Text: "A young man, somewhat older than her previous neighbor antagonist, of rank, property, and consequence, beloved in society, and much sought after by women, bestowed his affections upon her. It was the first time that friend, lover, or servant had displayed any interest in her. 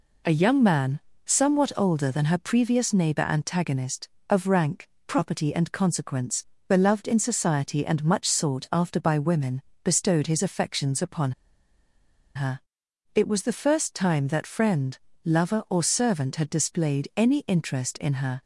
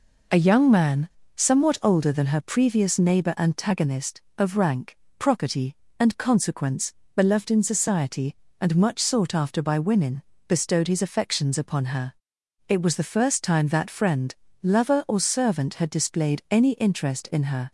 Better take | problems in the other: second | pauses between "upon" and "her"; at 11.3 s; 1.0 s long

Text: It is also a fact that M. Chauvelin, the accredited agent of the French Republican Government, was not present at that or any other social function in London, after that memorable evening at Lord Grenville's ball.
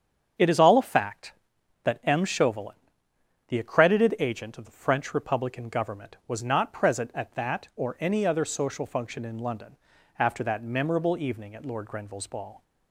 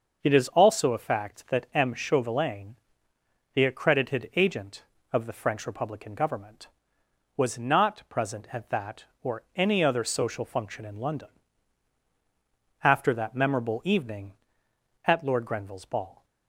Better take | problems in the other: second | starts louder than the rest; strong; until 1.9 s; 7.5 dB; noticeable in the second // says "all" for "also"; at 0.5 s

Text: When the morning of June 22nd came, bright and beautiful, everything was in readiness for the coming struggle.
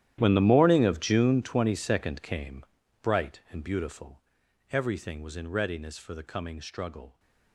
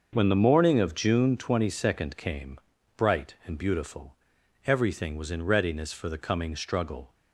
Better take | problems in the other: second | gets quieter; strong; throughout; 19 dB // starts louder than the rest; strong; until 1.2 s; 11.5 dB; also in the second

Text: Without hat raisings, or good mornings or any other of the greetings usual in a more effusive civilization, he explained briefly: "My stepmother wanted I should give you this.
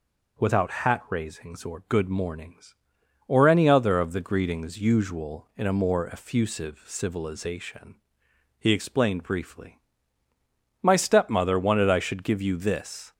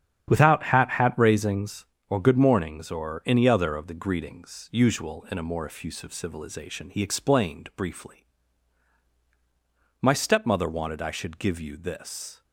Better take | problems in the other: first | starts louder than the rest; strong; until 1.3 s; 9 dB // says "hat" twice; at 0.9 s

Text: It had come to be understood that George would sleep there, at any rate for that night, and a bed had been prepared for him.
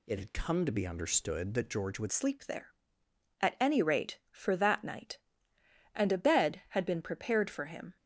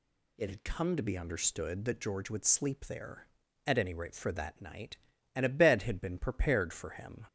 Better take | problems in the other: second | changes voice at "sleep"; from 2.1 s on; 5.8 s long

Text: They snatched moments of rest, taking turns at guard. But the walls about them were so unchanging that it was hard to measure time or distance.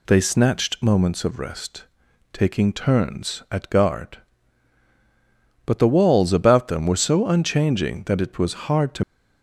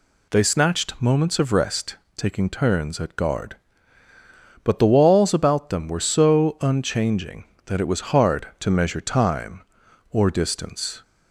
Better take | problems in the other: second | stops before "measure time or distance"; at 9.0 s

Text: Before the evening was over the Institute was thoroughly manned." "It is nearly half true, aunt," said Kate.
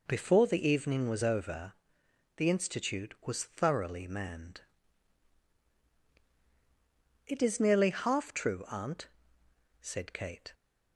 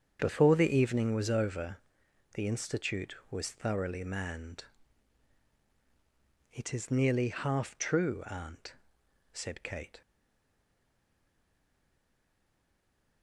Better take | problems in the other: first | starts louder than the rest; strong; until 1.2 s; 7.5 dB // pauses between "over" and "the"; noticeable; at 1.7 s; 0.56 s long; noticeable in the first // stays silent after the last word; strong; from 10.0 s on; 3.2 s long

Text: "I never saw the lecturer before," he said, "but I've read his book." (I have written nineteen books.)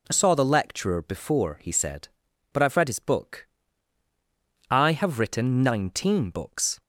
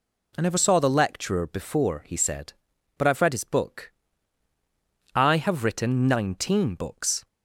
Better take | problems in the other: second | skips "never"; at 0.1 s

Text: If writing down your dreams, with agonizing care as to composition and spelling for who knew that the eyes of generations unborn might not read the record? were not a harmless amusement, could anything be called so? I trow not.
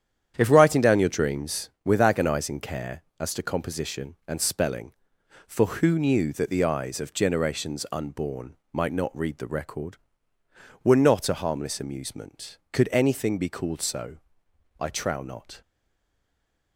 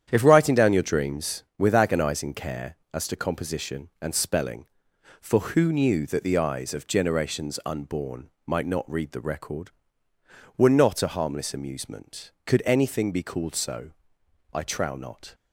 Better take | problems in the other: second | starts louder than the rest; strong; until 1.3 s; 9.5 dB; strong in the second // pauses between "unborn" and "might"; slight; at 8.5 s; 0.18 s long; slight in the second // stays silent after the last word; from 15.6 s on; 1.1 s long

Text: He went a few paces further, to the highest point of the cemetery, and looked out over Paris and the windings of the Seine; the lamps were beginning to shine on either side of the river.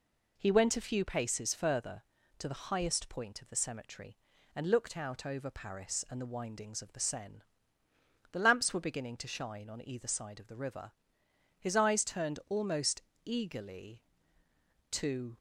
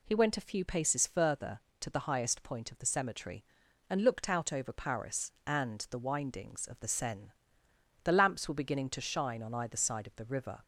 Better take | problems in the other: second | goes on to say "His eyes turned almost eagerly to"; strong; from 11.5 s on; 3.8 s long

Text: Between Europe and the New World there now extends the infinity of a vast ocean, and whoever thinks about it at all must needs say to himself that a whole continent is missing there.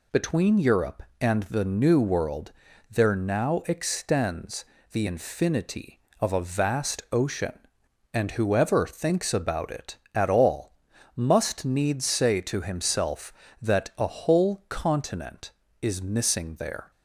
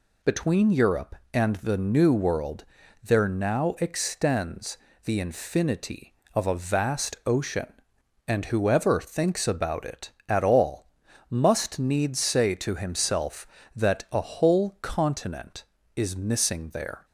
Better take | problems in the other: neither | pauses between "World" and "there"; the same in both // pauses between "extends" and "the"; slight; the same in both // pauses between "all" and "must"; the same in both

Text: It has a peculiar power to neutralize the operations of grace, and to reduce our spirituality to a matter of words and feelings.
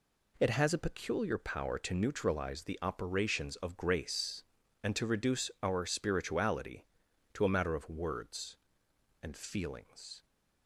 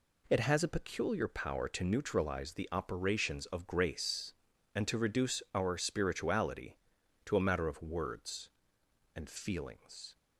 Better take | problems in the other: neither | none

